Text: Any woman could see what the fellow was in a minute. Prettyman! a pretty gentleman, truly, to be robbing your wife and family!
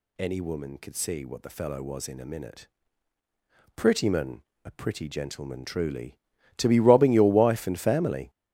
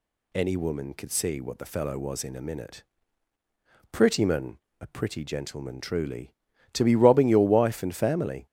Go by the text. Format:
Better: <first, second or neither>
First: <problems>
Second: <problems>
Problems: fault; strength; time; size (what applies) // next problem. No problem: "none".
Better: second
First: gets louder; strong; throughout; 10 dB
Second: none